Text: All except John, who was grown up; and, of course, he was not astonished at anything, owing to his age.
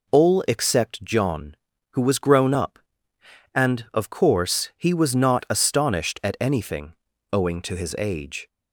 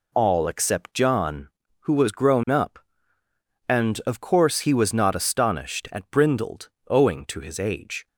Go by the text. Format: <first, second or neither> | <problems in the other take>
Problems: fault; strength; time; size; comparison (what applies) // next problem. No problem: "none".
first | says "brindled" for "anything"; at 6.0 s